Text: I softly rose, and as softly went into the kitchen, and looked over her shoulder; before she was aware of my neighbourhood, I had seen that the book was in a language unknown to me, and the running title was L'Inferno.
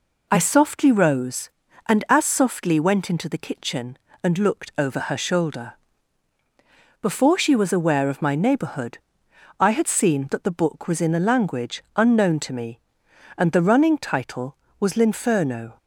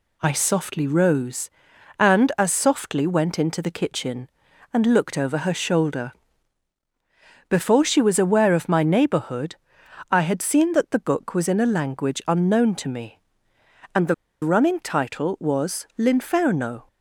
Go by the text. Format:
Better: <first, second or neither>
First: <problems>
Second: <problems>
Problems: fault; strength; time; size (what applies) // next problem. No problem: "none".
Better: first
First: none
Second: pauses between "the" and "running"; slight; at 14.1 s; 0.28 s long